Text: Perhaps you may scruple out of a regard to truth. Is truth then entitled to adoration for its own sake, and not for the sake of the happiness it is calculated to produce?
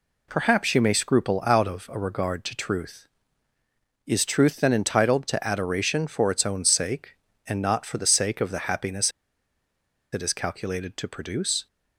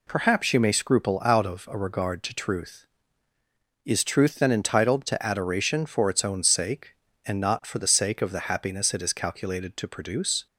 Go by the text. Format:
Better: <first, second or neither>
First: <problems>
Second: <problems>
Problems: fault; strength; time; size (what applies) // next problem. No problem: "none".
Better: second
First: pauses between "happiness" and "it"; at 9.1 s; 1.0 s long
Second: none